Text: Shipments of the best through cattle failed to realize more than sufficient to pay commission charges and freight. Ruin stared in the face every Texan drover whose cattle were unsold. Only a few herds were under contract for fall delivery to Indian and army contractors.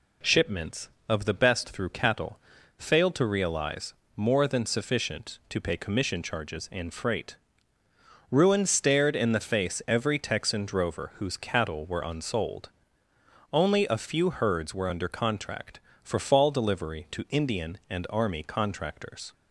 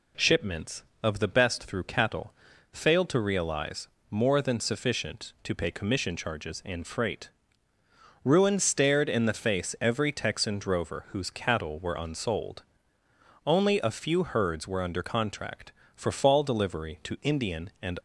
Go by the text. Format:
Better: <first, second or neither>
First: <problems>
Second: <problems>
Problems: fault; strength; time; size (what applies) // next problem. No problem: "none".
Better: first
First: pauses between "cattle" and "failed"; at 2.3 s; 0.40 s long // pauses between "realize" and "more"; slight; at 3.9 s; 0.22 s long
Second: pauses between "cattle" and "failed"; at 2.3 s; 0.40 s long // pauses between "realize" and "more"; slight; at 3.8 s; 0.22 s long // stops before "army contractors"; at 17.9 s